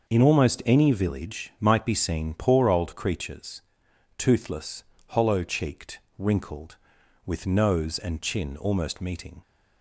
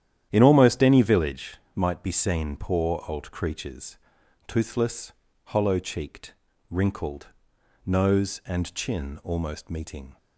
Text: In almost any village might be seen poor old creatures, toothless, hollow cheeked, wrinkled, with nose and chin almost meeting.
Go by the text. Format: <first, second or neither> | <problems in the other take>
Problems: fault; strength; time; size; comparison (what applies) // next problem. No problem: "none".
first | starts louder than the rest; strong; until 1.3 s; 10.5 dB; also in the first // pauses between "village" and "might"; slight; at 1.5 s; 0.18 s long // skips "with"; at 7.5 s